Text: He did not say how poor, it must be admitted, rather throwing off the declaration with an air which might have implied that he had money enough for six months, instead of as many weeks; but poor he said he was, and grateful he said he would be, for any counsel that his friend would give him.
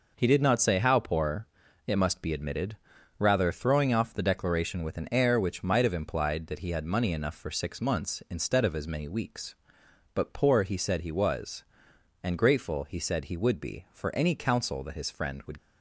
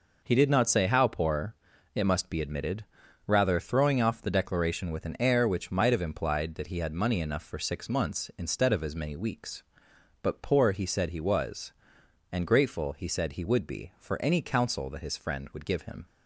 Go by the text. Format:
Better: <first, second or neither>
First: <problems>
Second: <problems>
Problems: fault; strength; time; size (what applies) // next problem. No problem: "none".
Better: second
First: stops before "give him"; at 15.5 s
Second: none